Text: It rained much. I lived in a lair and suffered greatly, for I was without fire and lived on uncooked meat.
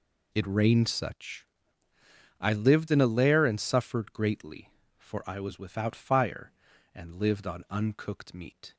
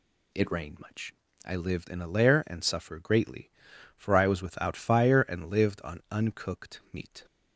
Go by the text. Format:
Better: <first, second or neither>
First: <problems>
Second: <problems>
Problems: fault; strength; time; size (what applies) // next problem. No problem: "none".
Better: second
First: says "such" for "much"; at 0.8 s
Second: none